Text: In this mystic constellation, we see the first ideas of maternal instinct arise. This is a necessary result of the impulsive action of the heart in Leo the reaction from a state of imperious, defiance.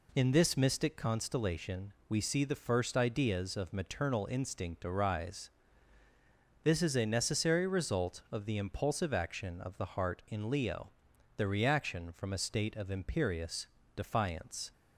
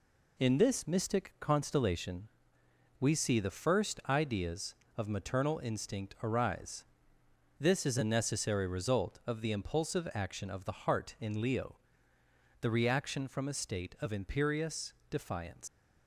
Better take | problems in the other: first | pauses between "Leo" and "the"; noticeable; at 11.7 s; 0.84 s long; noticeable in the first // leaves "defiance" unfinished; at 15.6 s; 110 ms

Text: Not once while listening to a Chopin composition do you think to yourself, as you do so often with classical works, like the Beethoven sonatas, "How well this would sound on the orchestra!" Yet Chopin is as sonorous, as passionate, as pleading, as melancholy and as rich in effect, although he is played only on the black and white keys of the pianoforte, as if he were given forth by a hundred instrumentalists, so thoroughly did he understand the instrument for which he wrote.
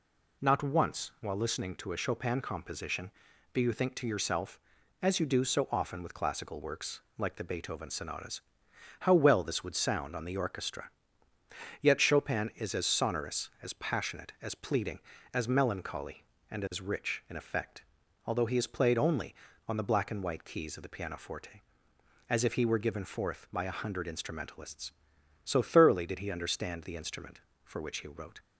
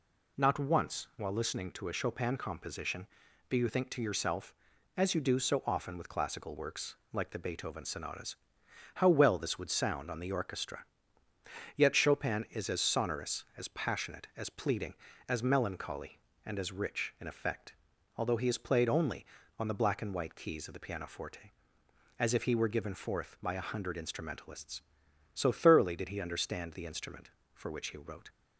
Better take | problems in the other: neither | none

